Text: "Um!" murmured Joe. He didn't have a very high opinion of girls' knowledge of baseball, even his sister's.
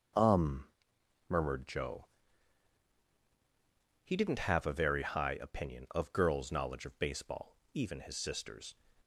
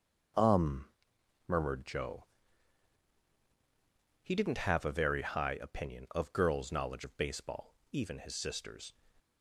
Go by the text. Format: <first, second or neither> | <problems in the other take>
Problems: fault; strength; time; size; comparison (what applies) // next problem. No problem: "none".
neither | starts louder than the rest; the same in both